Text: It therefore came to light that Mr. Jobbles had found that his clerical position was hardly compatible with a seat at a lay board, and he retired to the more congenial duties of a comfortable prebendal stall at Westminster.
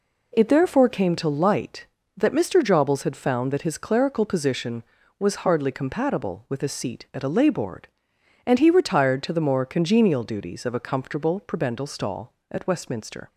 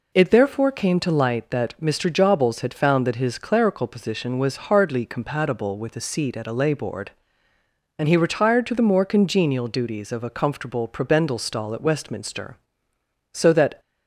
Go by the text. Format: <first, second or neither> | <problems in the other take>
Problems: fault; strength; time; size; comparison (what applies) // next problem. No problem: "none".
first | goes on to say "So that"; slight; from 13.3 s on; 0.48 s long